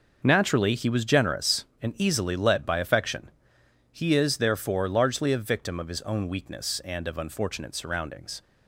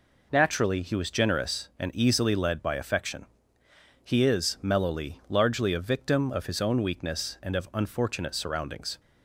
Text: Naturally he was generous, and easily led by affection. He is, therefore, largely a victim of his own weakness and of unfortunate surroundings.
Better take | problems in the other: first | says "mellowly" for "therefore"; at 4.6 s

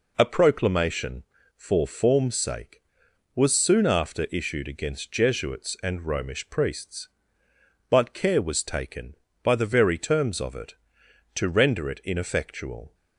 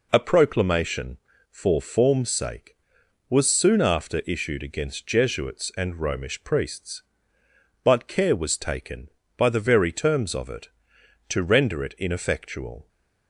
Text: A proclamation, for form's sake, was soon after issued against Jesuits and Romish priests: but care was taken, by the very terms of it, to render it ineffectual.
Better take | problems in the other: neither | none

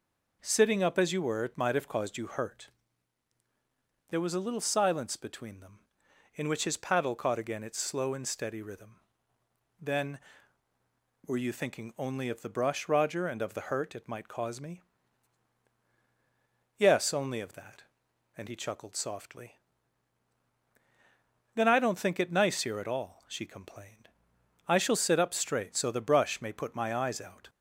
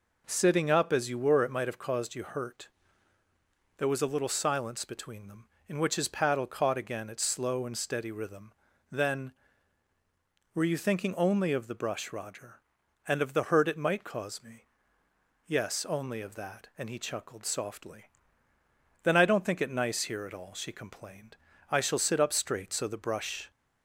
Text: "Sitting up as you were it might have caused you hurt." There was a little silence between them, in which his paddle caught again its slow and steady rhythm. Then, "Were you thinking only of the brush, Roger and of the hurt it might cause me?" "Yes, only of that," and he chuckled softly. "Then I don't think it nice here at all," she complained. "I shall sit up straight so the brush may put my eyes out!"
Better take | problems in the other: first | stops before "may put my eyes out"; at 23.5 s

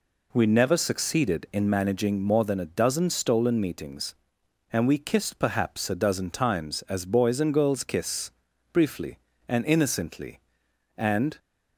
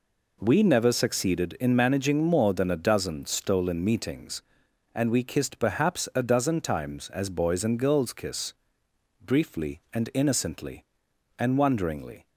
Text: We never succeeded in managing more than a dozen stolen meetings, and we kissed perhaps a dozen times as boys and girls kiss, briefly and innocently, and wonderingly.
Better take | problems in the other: second | stops before "wonderingly"; at 11.3 s

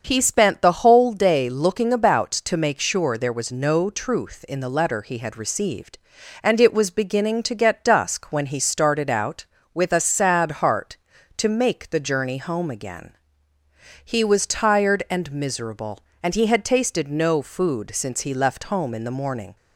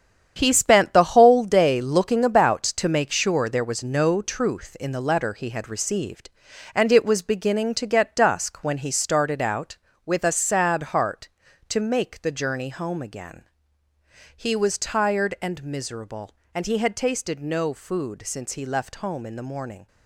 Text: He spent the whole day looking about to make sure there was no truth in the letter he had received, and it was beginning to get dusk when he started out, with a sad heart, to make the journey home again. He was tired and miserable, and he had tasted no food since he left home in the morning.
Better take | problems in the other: first | gets quieter; strong; throughout; 9.5 dB // starts louder than the rest; strong; until 1.3 s; 8.5 dB; also in the first

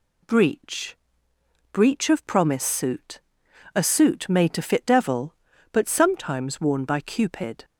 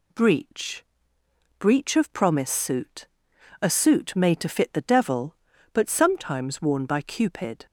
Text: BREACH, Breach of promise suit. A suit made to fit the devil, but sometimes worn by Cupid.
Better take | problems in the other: second | skips "the"; at 4.8 s

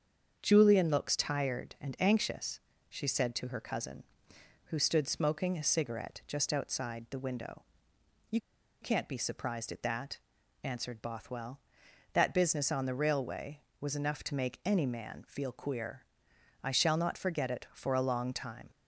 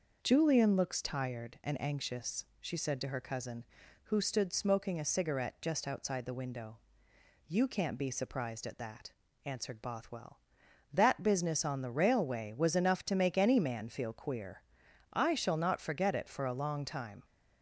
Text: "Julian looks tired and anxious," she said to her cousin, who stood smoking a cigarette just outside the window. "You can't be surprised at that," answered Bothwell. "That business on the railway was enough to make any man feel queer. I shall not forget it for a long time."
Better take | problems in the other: second | starts louder than the rest; strong; until 1.4 s; 7 dB // pauses between "You" and "can't"; at 8.3 s; 0.42 s long

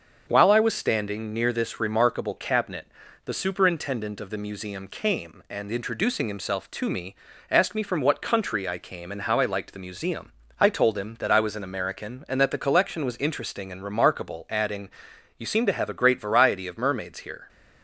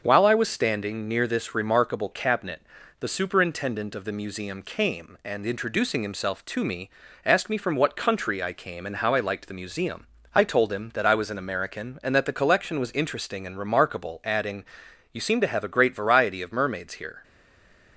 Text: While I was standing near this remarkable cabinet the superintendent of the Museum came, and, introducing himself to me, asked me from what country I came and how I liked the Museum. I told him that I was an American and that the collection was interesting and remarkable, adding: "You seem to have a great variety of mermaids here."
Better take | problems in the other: first | starts louder than the rest; until 1.0 s; 6.5 dB; also in the first // pauses between "cabinet" and "the"; at 2.6 s; 0.38 s long; also in the first // stays silent after the last word; slight; from 17.2 s on; 0.7 s long

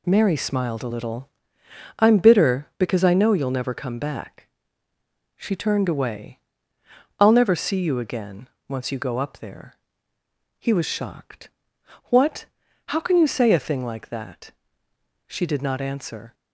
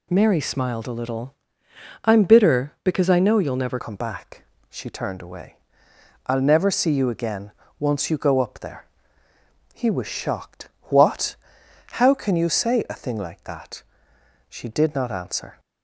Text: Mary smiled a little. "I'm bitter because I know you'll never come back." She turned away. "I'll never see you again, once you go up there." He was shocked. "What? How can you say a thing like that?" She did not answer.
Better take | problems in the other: first | changes voice at "come"; from 3.7 s on; 11.8 s long

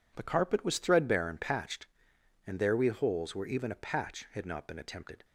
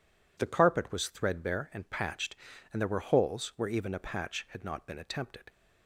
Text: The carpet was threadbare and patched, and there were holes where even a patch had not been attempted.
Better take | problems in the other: second | says "we" for "were"; at 2.7 s

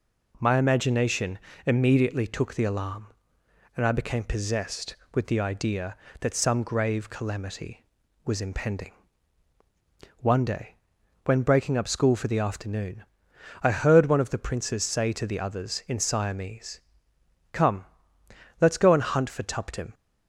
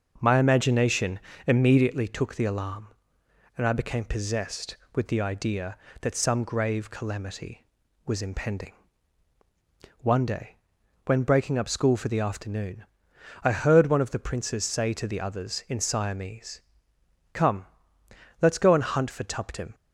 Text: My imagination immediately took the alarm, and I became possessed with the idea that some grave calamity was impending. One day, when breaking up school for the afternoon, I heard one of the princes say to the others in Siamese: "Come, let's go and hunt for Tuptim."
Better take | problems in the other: first | starts louder than the rest; until 2.0 s; 6.5 dB // pauses between "imagination" and "immediately"; slight; at 1.1 s; 0.28 s long; slight in the first

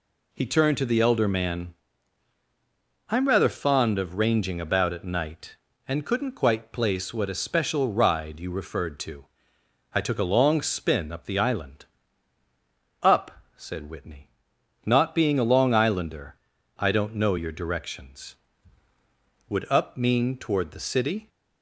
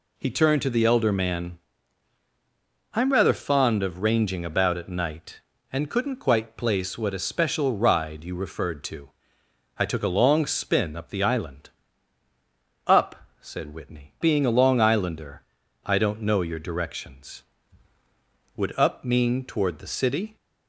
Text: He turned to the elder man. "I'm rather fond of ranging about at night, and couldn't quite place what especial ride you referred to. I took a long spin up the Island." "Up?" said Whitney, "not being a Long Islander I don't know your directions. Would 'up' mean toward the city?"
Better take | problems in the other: first | skips "not"; at 14.1 s // pauses between "Islander" and "I"; at 15.4 s; 0.44 s long; also in the first

